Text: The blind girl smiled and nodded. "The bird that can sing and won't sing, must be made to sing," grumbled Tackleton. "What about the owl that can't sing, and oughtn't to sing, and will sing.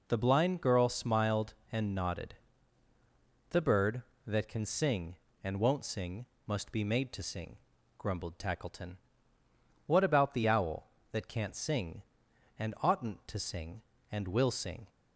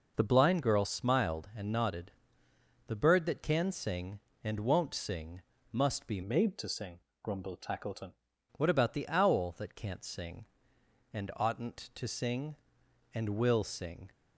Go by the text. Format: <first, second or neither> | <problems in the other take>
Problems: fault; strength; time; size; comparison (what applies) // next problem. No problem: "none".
first | changes voice from "made" to "Tackleton"; from 6.2 to 8.1 s; 1.9 s long